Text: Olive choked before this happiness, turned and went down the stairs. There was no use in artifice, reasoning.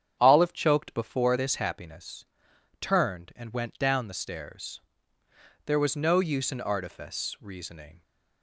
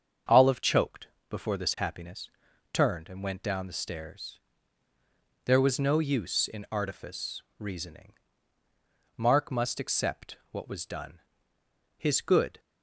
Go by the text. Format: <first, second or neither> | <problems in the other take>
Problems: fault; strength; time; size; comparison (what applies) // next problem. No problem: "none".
first | starts louder than the rest; until 1.5 s; 7 dB; strong in the first // pauses between "choked" and "before"; slight; at 1.0 s; 0.22 s long // goes on to say "Mark must accept what was done His good"; strong; from 9.1 s on; 3.4 s long